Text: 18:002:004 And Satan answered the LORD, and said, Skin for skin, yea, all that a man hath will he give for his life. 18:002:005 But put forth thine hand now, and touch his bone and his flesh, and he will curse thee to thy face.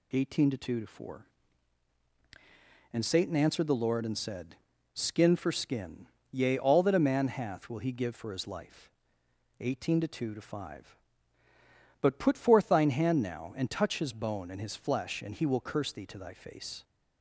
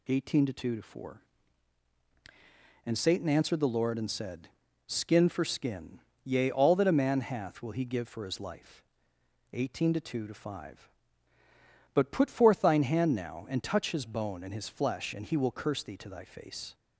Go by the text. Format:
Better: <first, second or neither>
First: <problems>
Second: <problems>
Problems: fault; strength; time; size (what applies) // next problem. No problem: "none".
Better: neither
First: none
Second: none